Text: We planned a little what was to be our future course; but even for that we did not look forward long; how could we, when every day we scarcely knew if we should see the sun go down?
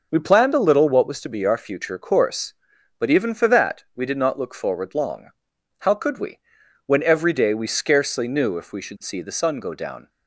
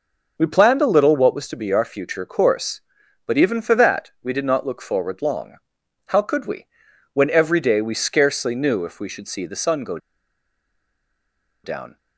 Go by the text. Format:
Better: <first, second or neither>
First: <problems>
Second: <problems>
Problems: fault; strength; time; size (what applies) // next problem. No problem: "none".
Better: first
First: none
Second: pauses between "go" and "down"; strong; at 9.9 s; 1.6 s long